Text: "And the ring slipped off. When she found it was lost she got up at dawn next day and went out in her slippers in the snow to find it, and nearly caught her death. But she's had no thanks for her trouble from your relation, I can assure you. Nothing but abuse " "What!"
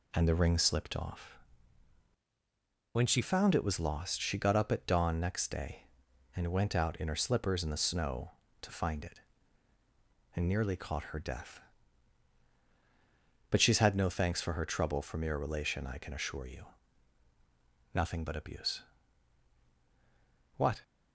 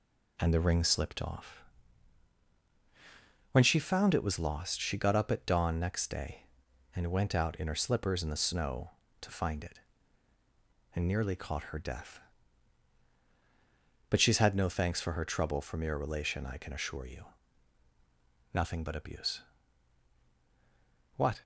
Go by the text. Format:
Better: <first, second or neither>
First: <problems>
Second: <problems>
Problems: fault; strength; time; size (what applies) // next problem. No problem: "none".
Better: second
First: changes voice from "When" to "she"; from 2.9 to 3.2 s; 0.3 s long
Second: none